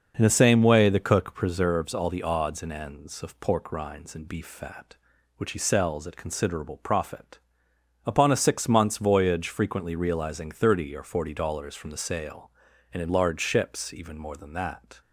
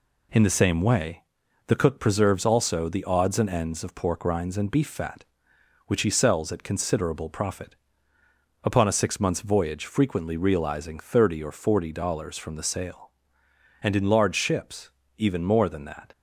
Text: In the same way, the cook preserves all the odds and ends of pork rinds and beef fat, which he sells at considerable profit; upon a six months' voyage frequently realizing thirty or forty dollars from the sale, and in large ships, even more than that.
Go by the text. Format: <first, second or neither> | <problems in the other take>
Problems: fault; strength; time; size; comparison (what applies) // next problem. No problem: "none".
first | says "also" for "all"; at 2.4 s